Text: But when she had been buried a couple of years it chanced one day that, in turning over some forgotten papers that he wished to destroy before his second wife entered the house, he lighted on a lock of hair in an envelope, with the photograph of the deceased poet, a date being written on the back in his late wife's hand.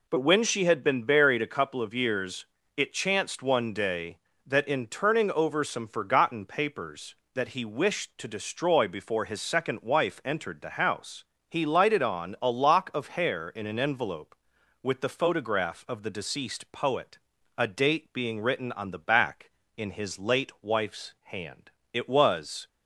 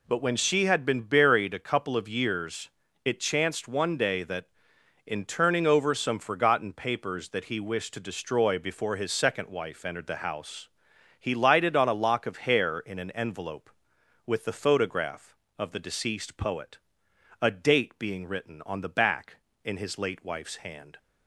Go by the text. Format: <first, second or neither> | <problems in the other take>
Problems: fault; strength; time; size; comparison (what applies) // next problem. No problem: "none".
second | pauses between "years" and "it"; slight; at 2.4 s; 0.32 s long; slight in the second // goes on to say "It was"; noticeable; from 21.9 s on; 0.76 s long